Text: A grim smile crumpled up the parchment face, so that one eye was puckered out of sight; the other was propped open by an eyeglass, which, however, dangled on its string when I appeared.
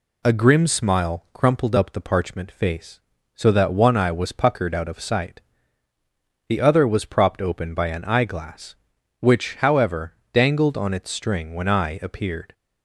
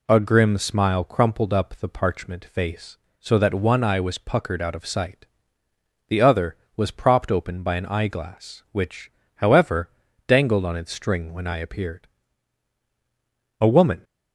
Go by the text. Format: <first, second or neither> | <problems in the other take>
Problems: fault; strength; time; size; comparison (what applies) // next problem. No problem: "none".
first | goes on to say "A woman"; slight; from 13.6 s on; 0.42 s long